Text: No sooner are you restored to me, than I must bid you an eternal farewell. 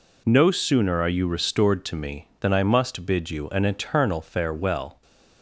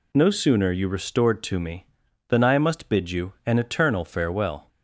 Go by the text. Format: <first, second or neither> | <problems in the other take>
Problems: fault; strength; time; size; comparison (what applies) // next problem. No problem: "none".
first | skips "are"; at 0.7 s